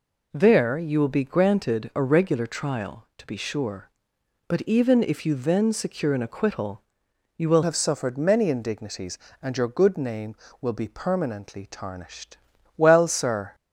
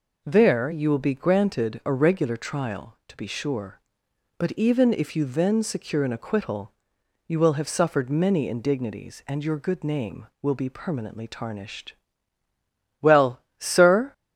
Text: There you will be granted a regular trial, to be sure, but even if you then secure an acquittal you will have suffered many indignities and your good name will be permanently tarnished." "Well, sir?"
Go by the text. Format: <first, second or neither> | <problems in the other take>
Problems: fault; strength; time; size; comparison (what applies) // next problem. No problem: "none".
second | pauses between "acquittal" and "you"; noticeable; at 6.8 s; 0.54 s long; noticeable in the second // changes voice at "have"; from 7.6 s on; 5.9 s long